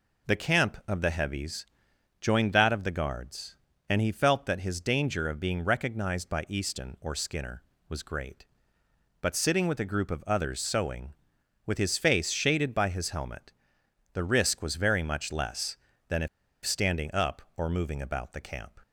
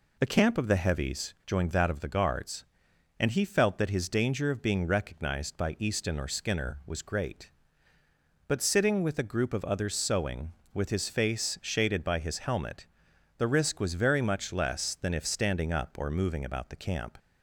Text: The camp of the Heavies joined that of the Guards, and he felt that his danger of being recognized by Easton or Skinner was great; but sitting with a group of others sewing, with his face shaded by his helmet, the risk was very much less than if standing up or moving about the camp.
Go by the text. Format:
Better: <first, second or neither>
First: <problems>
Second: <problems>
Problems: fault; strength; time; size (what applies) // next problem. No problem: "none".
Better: second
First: pauses between "Heavies" and "joined"; noticeable; at 1.6 s; 0.56 s long // pauses between "if" and "standing"; at 16.2 s; 0.36 s long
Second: none